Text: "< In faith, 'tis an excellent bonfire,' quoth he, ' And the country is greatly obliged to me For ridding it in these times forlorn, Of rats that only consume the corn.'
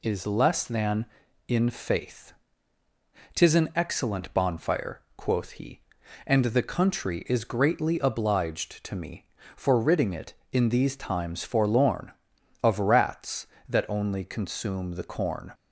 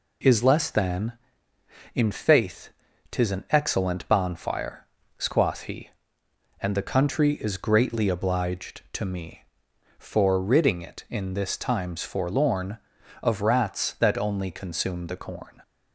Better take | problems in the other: first | says "this" for "these"; at 11.3 s

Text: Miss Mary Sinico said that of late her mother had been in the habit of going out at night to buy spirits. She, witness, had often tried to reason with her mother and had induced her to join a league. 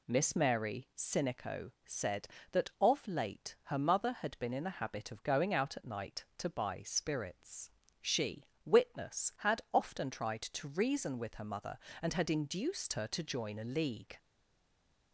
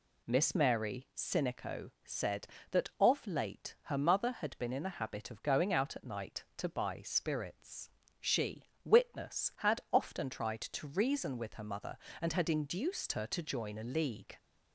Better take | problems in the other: second | stays silent after the last word; slight; from 14.1 s on; 1.0 s long

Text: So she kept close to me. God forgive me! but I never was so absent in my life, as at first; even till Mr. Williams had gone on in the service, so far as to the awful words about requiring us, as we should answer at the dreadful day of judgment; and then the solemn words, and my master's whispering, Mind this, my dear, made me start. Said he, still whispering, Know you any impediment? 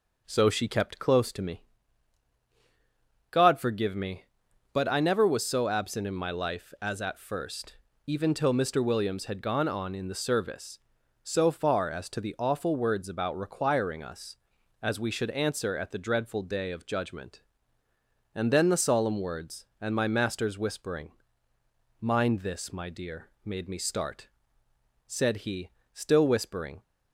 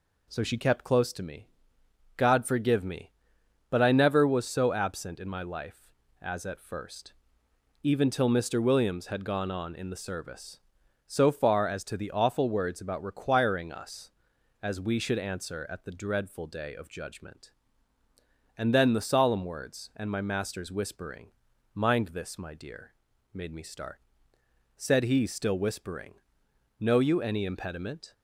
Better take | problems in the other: second | stops before "Know you any impediment"; at 26.8 s

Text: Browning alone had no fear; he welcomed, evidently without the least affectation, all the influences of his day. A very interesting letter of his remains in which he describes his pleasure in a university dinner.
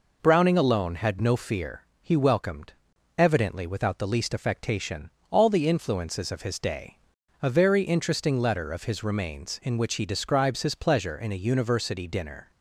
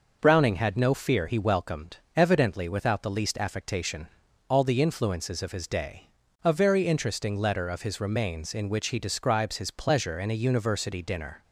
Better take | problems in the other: first | skips "alone"; at 0.5 s

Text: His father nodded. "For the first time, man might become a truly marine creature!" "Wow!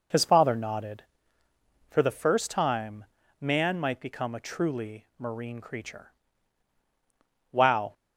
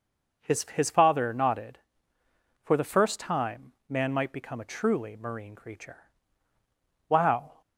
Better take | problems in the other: first | says "His" twice; at 0.7 s

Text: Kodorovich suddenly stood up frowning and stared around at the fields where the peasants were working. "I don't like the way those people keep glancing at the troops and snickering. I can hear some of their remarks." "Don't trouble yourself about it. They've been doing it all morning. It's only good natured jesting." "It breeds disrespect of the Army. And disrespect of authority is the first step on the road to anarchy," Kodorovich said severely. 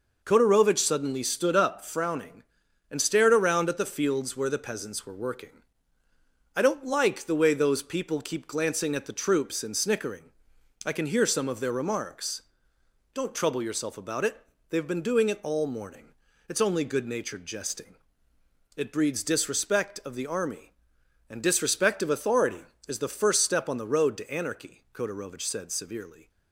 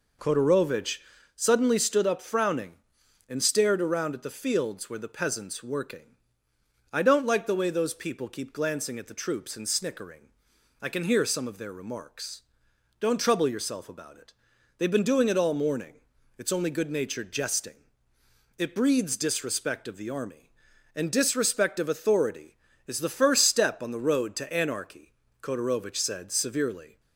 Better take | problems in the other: first | pauses between "Kodorovich" and "suddenly"; slight; at 0.9 s; 0.36 s long // skips "were"; at 5.6 s

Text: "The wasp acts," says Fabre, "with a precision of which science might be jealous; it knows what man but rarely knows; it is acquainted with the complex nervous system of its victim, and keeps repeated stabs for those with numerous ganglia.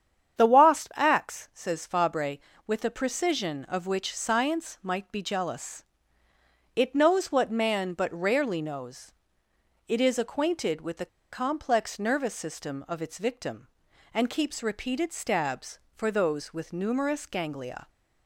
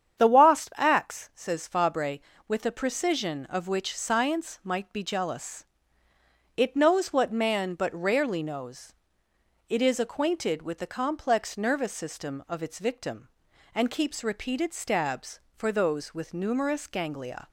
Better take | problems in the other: second | starts louder than the rest; strong; until 1.4 s; 8.5 dB; strong in the second // pauses between "the" and "complex"; slight; at 11.0 s; 0.25 s long

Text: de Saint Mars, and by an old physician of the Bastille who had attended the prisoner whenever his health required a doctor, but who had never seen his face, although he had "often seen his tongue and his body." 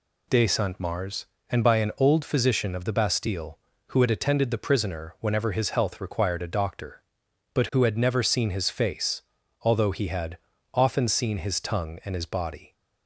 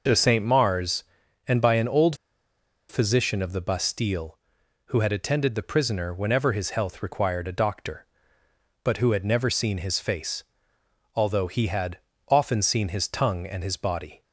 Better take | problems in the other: first | pauses between "old" and "physician"; noticeable; at 2.1 s; 0.74 s long // pauses between "had" and "often"; slight; at 11.9 s; 0.30 s long; slight in the first

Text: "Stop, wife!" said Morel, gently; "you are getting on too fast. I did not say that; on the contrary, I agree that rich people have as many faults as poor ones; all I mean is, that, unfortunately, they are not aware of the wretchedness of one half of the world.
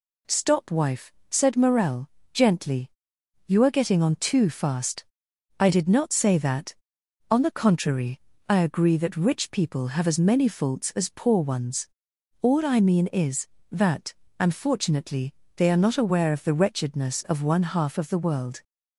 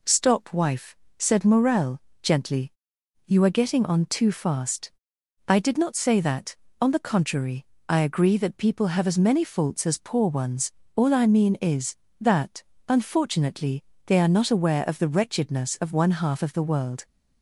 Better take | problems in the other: first | skips "rich"; at 8.5 s

